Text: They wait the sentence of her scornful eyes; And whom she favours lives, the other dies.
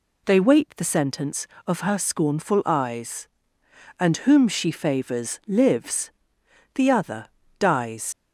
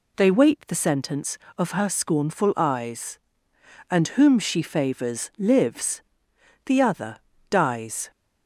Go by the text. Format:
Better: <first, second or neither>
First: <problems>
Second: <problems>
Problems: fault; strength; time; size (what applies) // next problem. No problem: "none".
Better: second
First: pauses between "other" and "dies"; slight; at 7.2 s; 0.34 s long // leaves "dies" unfinished; at 8.1 s; 70 ms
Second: pauses between "other" and "dies"; slight; at 7.1 s; 0.34 s long